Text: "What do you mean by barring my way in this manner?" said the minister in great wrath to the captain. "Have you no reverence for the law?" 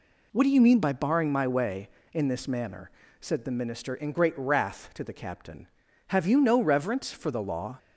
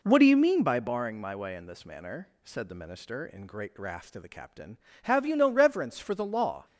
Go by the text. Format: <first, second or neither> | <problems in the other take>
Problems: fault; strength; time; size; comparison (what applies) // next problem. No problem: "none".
neither | none